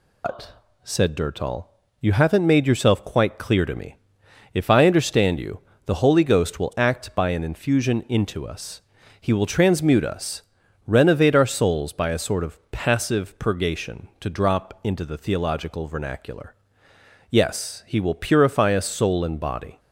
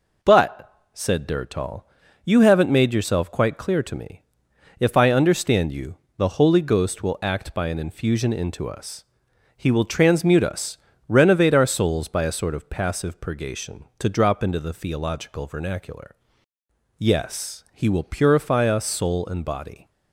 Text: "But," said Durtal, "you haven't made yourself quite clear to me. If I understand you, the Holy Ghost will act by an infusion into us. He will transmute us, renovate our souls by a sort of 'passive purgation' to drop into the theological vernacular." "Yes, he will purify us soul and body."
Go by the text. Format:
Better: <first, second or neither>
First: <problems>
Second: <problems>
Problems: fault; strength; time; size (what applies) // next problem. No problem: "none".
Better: second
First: loses the start of "But"; at 0.2 s; 155 ms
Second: none